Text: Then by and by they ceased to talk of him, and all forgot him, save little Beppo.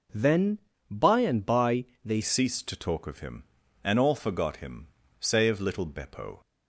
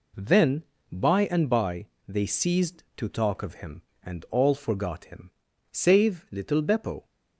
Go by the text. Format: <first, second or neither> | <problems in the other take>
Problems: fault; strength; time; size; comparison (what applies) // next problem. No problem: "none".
second | pauses between "by" and "they"; slight; at 1.8 s; 0.20 s long; slight in the second // changes voice at "ceased"; from 2.2 s on; 4.2 s long